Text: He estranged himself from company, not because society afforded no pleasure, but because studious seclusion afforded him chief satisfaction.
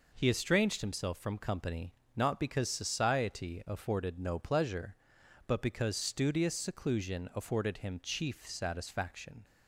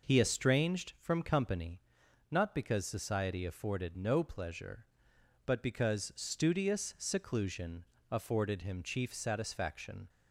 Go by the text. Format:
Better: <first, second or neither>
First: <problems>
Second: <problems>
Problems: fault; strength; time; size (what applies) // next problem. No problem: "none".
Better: first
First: none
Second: skips "himself"; at 0.9 s // pauses between "seclusion" and "afforded"; slight; at 7.8 s; 0.26 s long